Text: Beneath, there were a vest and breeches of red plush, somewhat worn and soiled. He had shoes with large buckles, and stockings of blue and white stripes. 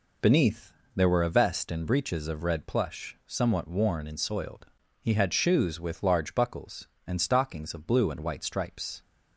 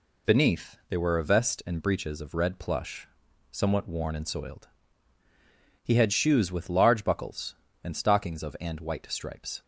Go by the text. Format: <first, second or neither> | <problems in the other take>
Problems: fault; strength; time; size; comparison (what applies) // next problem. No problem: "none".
first | skips "blue"; at 8.5 s